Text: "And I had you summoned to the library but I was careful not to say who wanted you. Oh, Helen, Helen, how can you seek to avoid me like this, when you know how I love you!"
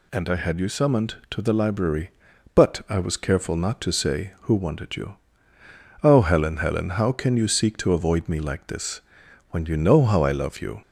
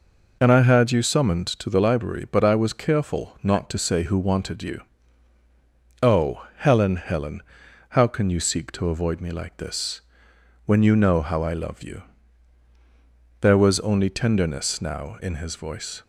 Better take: first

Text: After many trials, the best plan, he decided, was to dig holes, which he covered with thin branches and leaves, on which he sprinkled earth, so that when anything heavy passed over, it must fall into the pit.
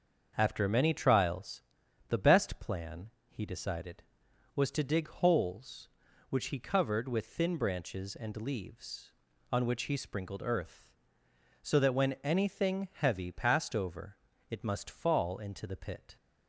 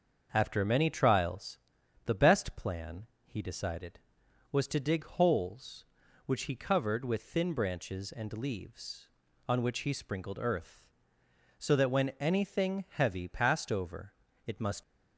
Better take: first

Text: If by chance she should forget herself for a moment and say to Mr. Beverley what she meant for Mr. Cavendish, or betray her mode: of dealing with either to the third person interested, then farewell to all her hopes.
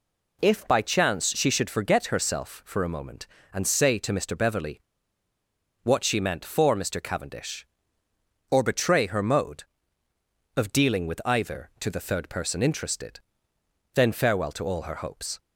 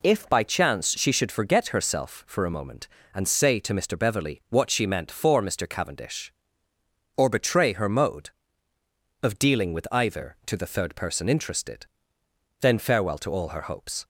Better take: second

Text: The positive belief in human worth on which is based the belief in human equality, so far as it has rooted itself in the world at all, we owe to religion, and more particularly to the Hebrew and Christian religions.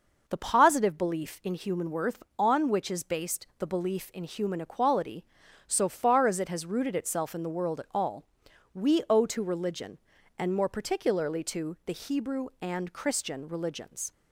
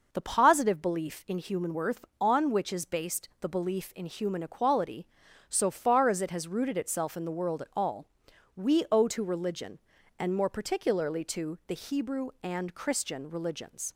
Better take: neither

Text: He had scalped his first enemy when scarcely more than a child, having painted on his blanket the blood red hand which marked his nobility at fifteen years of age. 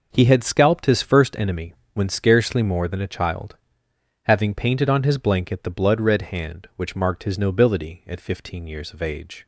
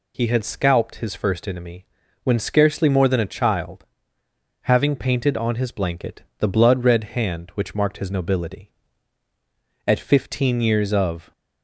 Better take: first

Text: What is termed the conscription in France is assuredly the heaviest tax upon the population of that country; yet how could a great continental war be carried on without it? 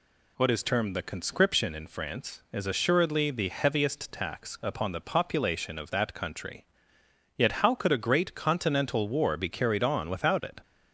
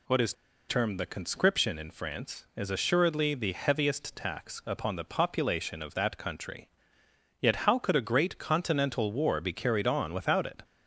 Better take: first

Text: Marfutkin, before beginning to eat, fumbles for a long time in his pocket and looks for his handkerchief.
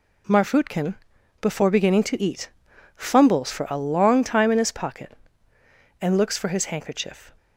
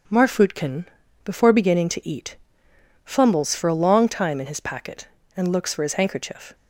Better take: first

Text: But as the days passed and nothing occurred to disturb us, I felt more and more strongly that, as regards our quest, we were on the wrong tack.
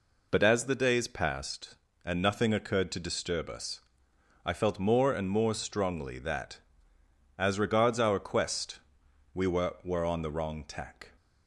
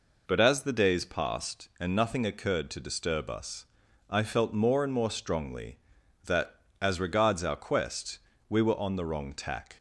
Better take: second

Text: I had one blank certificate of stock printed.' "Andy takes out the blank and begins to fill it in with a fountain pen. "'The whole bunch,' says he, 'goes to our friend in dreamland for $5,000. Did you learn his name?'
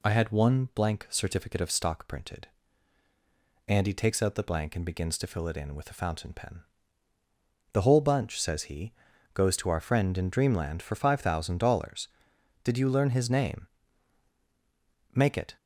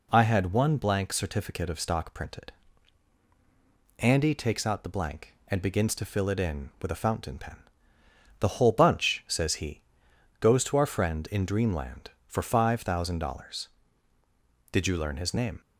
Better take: second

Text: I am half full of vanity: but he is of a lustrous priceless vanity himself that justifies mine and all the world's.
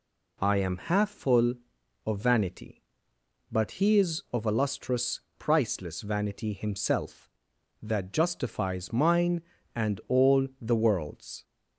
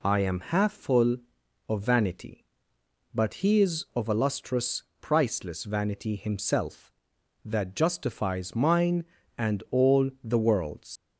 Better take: first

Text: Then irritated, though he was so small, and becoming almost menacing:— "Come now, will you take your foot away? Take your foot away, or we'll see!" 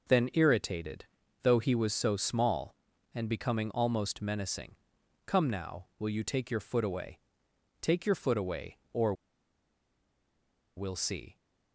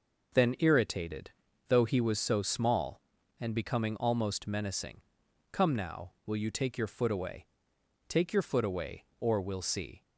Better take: second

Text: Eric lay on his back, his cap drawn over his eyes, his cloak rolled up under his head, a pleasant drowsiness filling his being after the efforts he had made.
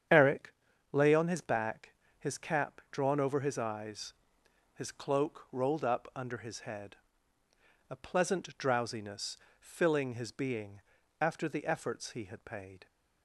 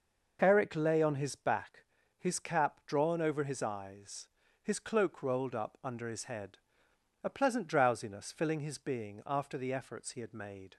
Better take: second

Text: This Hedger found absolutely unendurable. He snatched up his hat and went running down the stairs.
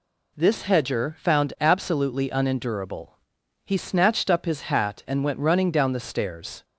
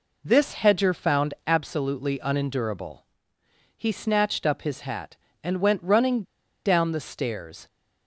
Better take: first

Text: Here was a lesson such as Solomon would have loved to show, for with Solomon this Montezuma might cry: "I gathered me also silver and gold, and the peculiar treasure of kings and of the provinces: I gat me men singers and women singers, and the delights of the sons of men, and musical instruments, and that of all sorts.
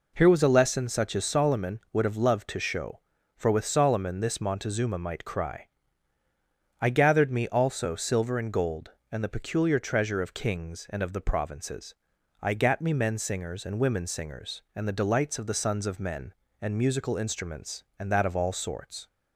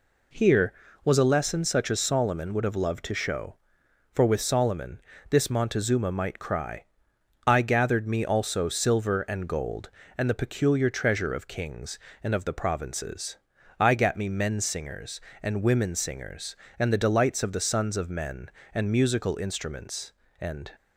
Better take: first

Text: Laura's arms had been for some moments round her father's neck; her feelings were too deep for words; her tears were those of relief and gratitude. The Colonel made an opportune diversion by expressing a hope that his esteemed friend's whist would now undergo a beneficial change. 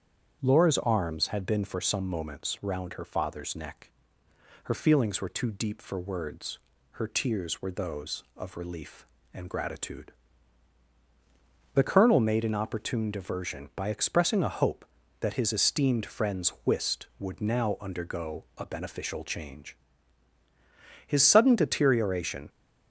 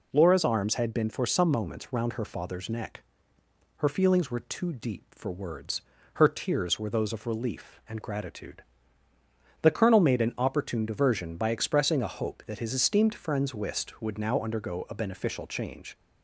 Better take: second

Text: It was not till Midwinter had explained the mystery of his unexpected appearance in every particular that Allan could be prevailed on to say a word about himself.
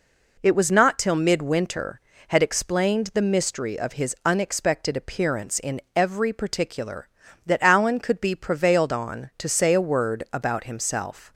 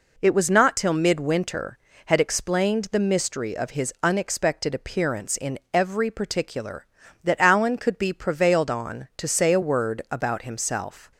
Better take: neither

